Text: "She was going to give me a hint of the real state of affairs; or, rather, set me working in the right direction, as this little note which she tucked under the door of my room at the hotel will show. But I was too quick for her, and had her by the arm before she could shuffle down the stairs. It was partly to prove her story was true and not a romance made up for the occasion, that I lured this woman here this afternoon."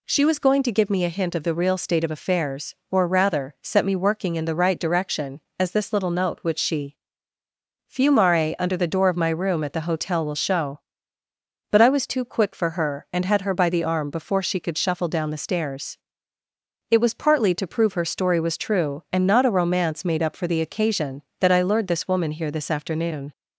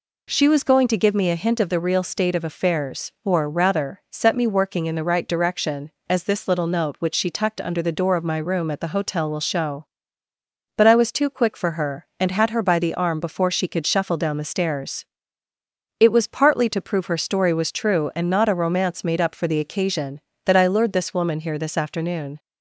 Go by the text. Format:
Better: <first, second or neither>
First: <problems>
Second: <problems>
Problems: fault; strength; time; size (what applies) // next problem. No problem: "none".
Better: second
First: says "fumare" for "tucked"; at 7.8 s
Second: none